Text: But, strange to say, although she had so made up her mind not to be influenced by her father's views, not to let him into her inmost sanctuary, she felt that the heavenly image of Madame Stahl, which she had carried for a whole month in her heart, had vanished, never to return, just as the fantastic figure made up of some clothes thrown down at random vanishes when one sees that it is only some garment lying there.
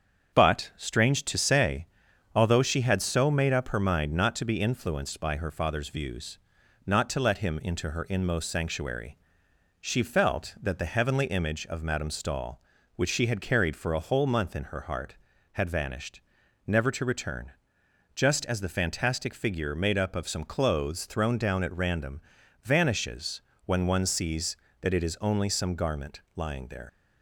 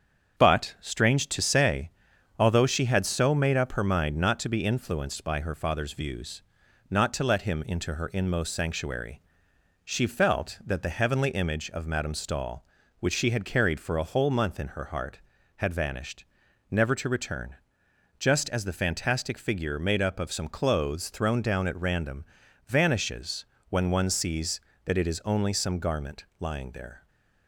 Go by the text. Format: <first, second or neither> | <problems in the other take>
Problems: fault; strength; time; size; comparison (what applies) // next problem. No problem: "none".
second | starts louder than the rest; strong; until 1.4 s; 7.5 dB; strong in the second // pauses between "random" and "vanishes"; at 22.2 s; 0.42 s long; also in the second // pauses between "vanishes" and "when"; slight; at 23.4 s; 0.24 s long; slight in the second // leaves "there" unfinished; at 26.8 s; 135 ms